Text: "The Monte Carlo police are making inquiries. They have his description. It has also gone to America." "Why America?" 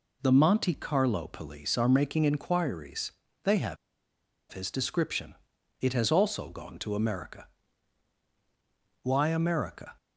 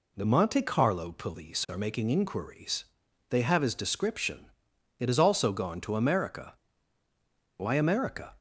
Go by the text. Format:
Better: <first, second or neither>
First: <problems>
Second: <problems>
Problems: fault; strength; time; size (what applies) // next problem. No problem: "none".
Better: second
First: pauses between "have" and "his"; noticeable; at 3.7 s; 0.75 s long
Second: none